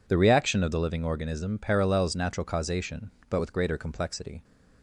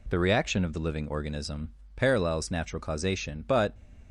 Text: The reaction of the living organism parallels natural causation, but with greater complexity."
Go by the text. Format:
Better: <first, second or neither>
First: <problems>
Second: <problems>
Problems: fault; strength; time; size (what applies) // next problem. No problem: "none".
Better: first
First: none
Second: pauses between "organism" and "parallels"; slight; at 1.7 s; 0.24 s long // stops before "with greater complexity"; at 3.7 s